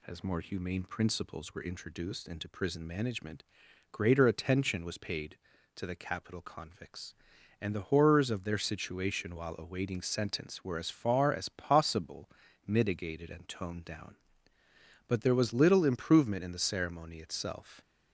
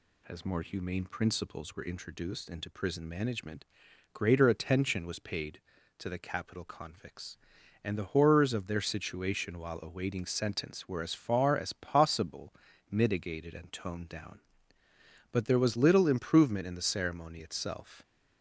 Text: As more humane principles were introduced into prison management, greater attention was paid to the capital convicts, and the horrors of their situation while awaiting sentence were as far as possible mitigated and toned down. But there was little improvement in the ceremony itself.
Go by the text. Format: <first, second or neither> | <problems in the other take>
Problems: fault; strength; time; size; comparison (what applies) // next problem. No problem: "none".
neither | pauses between "possible" and "mitigated"; slight; the same in both